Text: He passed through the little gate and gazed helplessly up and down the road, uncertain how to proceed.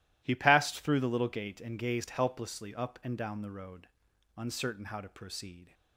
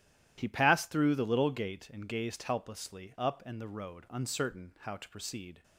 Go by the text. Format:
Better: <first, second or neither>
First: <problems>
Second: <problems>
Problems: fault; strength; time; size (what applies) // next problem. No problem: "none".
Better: first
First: none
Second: starts louder than the rest; strong; until 1.3 s; 12 dB // skips "down"; at 3.6 s